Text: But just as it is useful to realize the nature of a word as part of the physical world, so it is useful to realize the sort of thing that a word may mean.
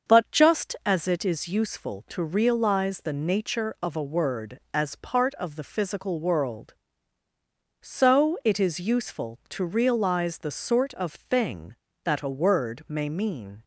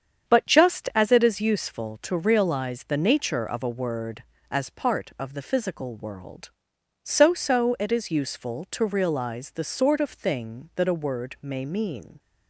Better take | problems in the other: first | starts louder than the rest; strong; until 1.3 s; 7.5 dB; also in the first // says "so" twice; at 7.3 s

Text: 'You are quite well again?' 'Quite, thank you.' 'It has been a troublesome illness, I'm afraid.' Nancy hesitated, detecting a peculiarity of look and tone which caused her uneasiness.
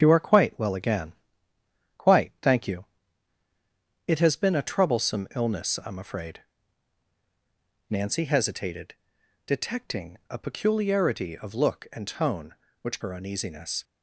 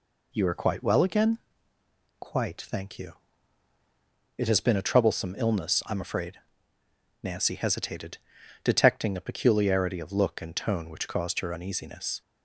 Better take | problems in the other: second | starts louder than the rest; strong; until 1.0 s; 8 dB // skips "caused"; at 12.9 s

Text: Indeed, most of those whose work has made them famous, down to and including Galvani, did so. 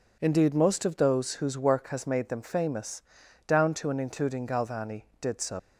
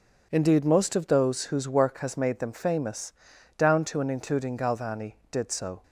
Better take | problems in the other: second | leaves "so" unfinished; at 5.5 s; 125 ms

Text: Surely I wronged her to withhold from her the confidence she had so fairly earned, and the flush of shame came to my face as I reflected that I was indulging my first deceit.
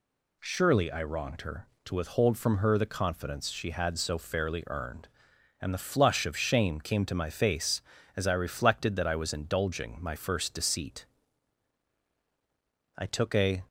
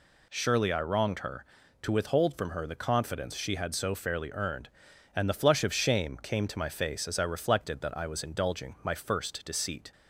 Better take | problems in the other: second | goes on to say "I took a"; noticeable; from 12.9 s on; 0.70 s long

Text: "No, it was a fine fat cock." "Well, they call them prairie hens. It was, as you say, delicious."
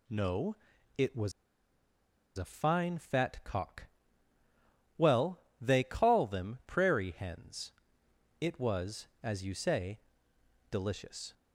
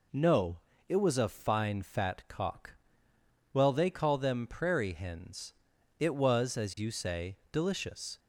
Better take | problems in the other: second | pauses between "was" and "a"; at 1.3 s; 1.0 s long

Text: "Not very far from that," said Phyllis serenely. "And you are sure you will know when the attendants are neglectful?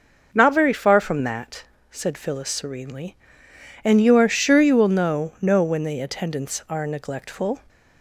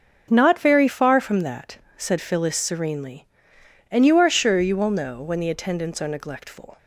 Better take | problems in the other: second | starts louder than the rest; noticeable; until 1.3 s; 6 dB; also in the second // says "know" twice; at 5.3 s

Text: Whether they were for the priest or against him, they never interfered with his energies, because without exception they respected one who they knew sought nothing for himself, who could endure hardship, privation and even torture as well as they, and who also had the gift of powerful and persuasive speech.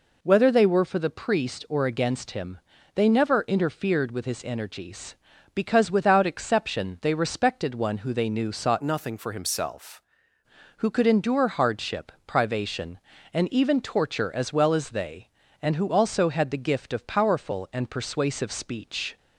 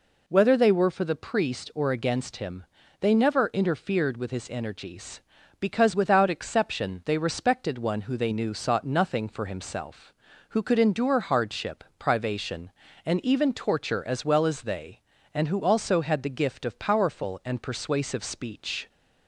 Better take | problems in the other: second | changes voice from "nothing" to "himself"; from 8.8 to 10.0 s; 1.2 s long

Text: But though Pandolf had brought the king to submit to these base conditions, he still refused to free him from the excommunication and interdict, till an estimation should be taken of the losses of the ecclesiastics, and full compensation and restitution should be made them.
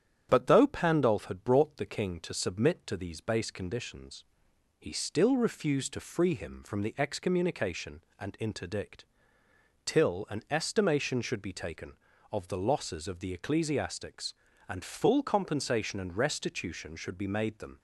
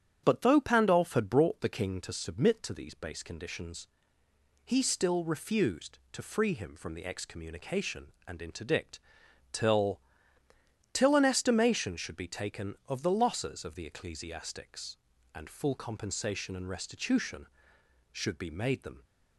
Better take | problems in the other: first | starts louder than the rest; strong; until 1.2 s; 8.5 dB; strong in the first // says "till" twice; at 10.9 s

